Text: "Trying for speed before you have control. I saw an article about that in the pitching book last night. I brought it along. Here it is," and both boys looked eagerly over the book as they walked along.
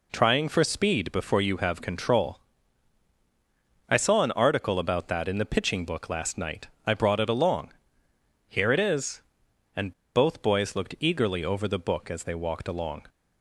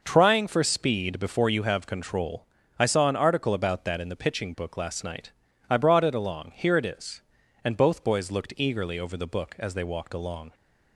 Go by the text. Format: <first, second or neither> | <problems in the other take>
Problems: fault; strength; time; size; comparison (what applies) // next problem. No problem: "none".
second | pauses between "and" and "both"; slight; at 9.9 s; 0.23 s long